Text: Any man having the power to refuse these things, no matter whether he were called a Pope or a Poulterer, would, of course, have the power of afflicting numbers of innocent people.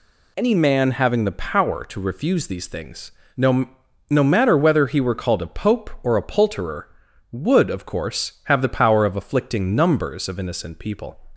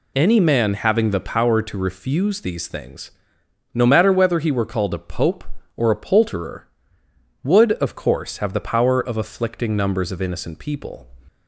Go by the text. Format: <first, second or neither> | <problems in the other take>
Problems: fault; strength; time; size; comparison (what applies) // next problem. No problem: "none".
second | says "no" twice; at 4.0 s